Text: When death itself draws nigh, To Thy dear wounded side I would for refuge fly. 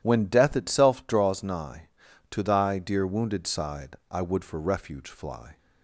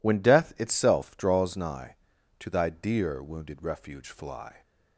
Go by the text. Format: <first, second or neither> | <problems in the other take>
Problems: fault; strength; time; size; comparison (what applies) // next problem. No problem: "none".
first | skips "side I would for"; at 3.6 s